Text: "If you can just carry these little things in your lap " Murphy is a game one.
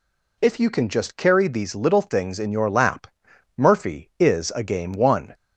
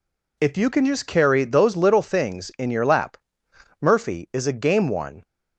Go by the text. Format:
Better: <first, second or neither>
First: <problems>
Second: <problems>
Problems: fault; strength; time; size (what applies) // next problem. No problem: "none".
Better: first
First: none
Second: says "those" for "these"; at 1.4 s